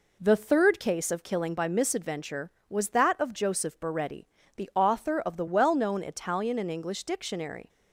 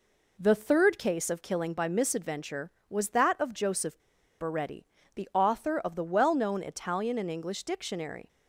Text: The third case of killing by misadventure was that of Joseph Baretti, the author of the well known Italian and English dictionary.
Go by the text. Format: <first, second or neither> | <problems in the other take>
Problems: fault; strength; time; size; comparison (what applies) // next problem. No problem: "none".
first | pauses between "Joseph" and "Baretti"; at 3.9 s; 0.40 s long